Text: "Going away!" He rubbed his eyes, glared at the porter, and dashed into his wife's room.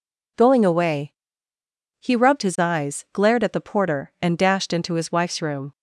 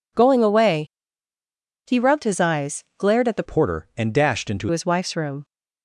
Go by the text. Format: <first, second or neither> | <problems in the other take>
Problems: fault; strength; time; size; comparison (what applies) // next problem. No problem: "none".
first | changes voice from "porter" to "into"; from 3.4 to 4.6 s; 1.2 s long